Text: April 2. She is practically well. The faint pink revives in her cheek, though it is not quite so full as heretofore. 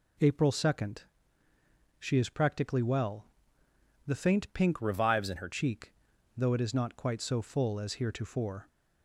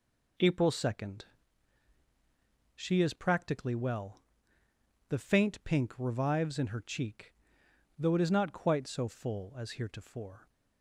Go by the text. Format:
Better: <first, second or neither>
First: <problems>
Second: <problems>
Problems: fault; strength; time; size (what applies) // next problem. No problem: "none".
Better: second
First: changes voice from "revives" to "her"; from 4.8 to 5.4 s; 0.6 s long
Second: none